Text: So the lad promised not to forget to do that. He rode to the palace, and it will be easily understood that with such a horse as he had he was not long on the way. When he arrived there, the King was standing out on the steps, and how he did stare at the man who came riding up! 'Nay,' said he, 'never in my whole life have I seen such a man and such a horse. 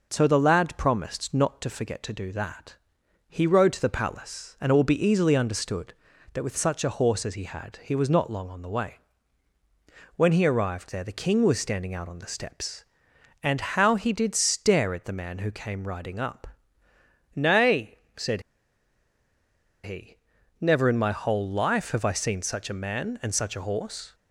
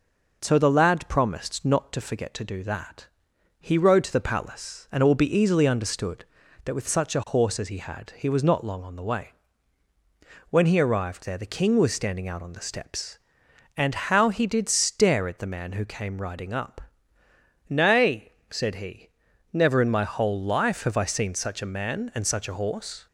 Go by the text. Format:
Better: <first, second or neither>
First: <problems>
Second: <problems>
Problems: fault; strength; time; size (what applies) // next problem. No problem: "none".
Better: second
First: pauses between "said" and "he"; strong; at 18.4 s; 1.4 s long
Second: none